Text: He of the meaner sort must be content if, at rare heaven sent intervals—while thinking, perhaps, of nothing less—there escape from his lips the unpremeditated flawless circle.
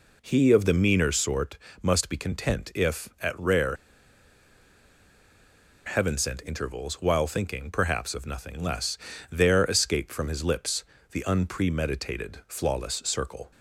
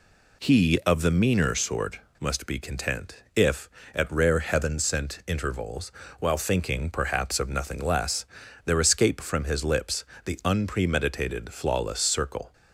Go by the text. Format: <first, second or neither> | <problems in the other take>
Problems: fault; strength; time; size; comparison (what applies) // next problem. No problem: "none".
second | pauses between "sort" and "must"; slight; at 1.5 s; 0.24 s long; slight in the second // pauses between "rare" and "heaven"; strong; at 3.7 s; 2.1 s long // pauses between "lips" and "the"; slight; at 10.8 s; 0.28 s long; slight in the second